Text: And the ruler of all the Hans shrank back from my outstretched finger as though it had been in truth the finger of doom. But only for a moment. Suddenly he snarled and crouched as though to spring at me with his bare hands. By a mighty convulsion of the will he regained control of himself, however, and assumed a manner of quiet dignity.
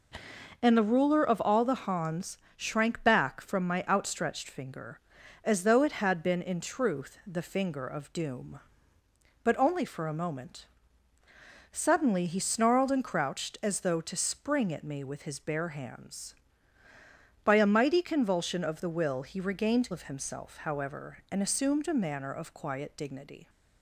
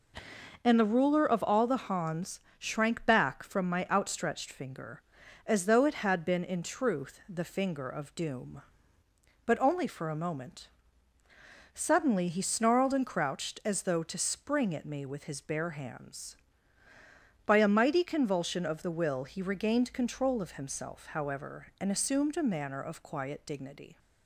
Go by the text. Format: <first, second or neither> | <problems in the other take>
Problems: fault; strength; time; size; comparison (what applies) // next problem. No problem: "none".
second | pauses between "Hans" and "shrank"; slight; at 2.3 s; 0.20 s long; slight in the second // skips "control"; at 19.9 s